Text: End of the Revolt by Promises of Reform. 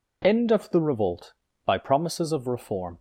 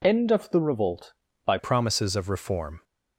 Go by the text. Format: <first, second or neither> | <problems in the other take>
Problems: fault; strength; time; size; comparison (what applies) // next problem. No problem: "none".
first | changes voice at "Promises"; from 1.5 s on; 1.3 s long